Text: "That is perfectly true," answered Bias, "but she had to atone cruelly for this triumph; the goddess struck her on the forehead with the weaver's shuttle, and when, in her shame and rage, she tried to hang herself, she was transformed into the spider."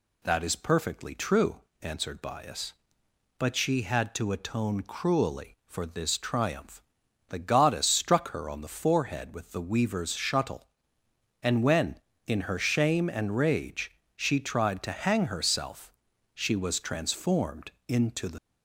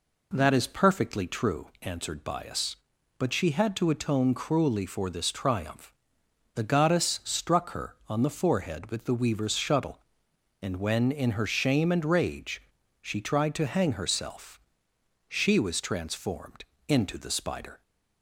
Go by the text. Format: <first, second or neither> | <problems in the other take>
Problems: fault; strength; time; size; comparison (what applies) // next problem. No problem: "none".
second | pauses between "transformed" and "into"; slight; at 17.7 s; 0.16 s long; slight in the second // stops before "spider"; at 18.3 s